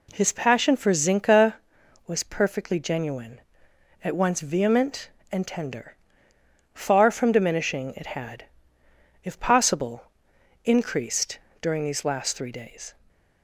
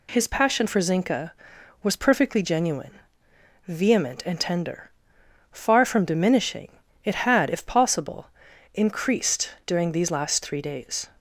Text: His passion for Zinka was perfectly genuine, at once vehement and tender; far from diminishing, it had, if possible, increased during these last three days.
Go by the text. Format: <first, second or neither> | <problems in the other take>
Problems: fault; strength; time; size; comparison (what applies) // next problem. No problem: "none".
first | skips "at once"; at 3.3 s // pauses between "increased" and "during"; slight; at 9.5 s; 0.16 s long; slight in the first